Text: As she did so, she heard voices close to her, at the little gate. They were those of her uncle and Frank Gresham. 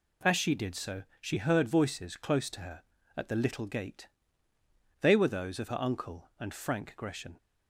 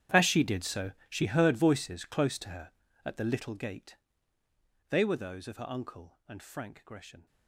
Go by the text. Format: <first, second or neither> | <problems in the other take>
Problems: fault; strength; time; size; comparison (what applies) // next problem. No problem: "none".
first | gets quieter; strong; throughout; 18.5 dB